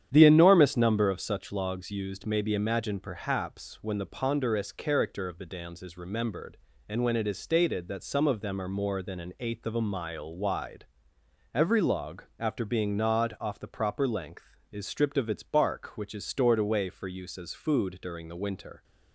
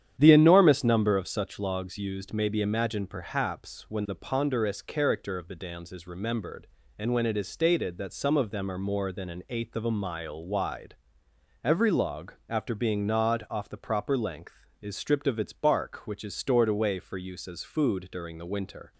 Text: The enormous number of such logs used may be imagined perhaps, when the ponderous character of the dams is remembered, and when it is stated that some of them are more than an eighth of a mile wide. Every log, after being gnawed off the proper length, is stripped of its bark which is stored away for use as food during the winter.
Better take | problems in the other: neither | starts louder than the rest; strong; the same in both

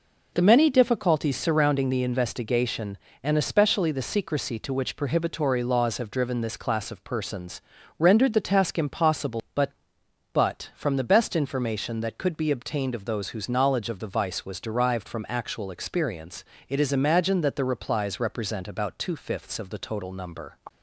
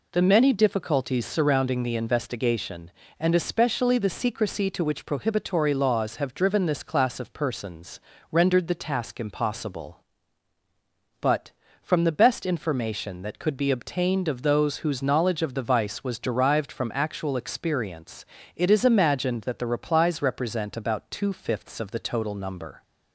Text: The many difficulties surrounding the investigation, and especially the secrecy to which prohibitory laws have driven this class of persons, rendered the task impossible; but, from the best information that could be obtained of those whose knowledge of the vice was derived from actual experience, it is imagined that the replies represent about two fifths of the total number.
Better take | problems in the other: second | says "but" twice; at 10.3 s

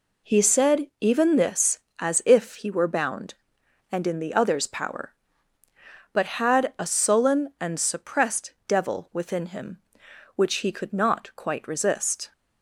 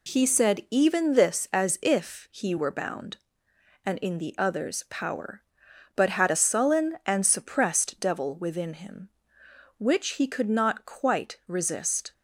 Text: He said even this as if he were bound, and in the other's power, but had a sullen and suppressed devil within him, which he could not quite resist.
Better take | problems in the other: neither | none

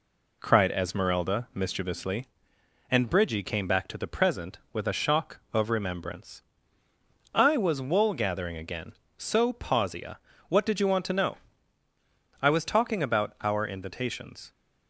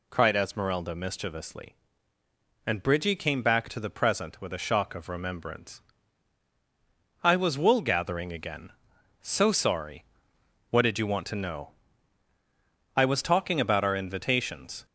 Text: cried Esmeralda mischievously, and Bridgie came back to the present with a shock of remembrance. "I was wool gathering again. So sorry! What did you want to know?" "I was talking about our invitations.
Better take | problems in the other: second | says "pausia" for "sorry"; at 9.5 s

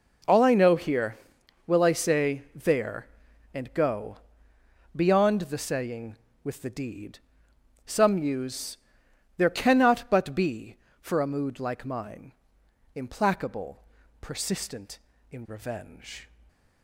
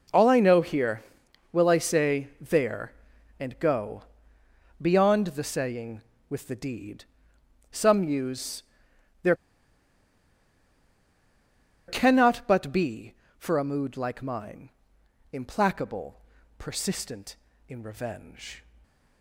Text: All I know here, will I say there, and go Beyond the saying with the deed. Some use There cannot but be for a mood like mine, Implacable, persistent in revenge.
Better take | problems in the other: first | pauses between "go" and "Beyond"; noticeable; at 4.0 s; 0.78 s long; noticeable in the first // pauses between "use" and "There"; noticeable; at 8.6 s; 0.58 s long; noticeable in the first // pauses between "There" and "cannot"; strong; at 9.3 s; 2.5 s long

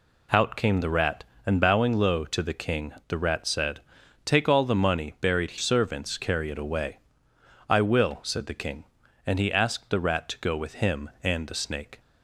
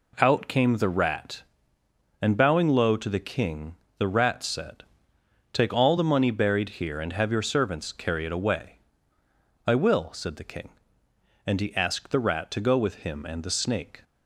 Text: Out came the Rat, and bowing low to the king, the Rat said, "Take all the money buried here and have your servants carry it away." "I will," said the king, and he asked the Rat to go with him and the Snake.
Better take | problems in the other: second | skips "here and have your"; at 5.5 s

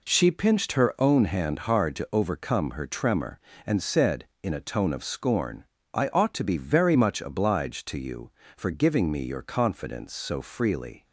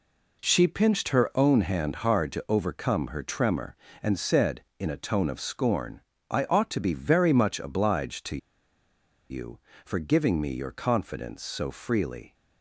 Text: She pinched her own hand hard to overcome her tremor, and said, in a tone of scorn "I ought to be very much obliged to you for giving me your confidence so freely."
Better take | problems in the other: first | pauses between "scorn" and "I"; slight; at 5.9 s; 0.32 s long; slight in the first // pauses between "to" and "you"; noticeable; at 8.3 s; 0.93 s long

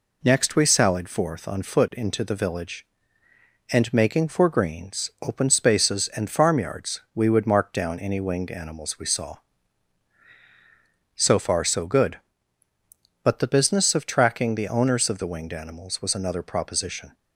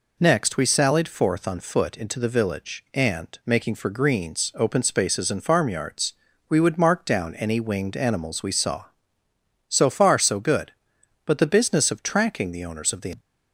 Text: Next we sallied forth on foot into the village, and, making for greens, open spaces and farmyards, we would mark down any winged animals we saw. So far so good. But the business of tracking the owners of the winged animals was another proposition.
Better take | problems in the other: first | stops before "winged animals was another proposition"; at 13.1 s

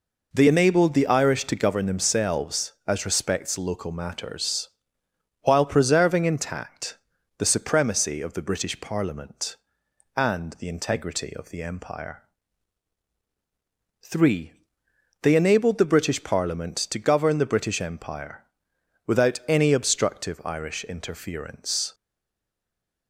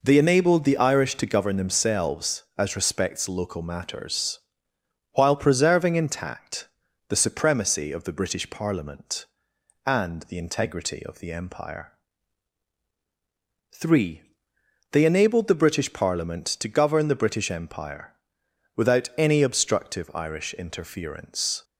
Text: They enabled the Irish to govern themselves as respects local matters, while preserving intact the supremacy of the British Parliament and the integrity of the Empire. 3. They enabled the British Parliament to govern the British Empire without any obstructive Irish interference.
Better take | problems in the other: second | pauses between "intact" and "the"; at 6.9 s; 0.40 s long; also in the second // pauses between "Empire" and "without"; noticeable; at 18.4 s; 0.62 s long; noticeable in the second // stays silent after the last word; noticeable; from 21.9 s on; 1.1 s long

